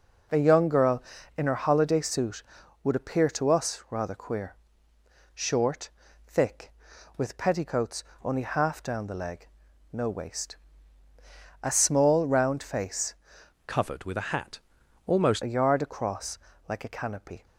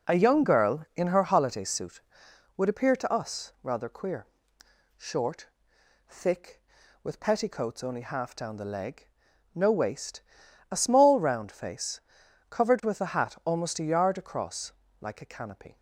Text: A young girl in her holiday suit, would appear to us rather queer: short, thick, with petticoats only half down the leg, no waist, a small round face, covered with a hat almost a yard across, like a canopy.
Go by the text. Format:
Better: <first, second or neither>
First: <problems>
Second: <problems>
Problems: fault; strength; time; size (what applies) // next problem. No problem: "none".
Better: second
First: pauses between "petticoats" and "only"; slight; at 8.0 s; 0.18 s long // changes voice from "covered" to "almost"; from 13.6 to 15.4 s; 1.8 s long // pauses between "hat" and "almost"; noticeable; at 14.5 s; 0.46 s long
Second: none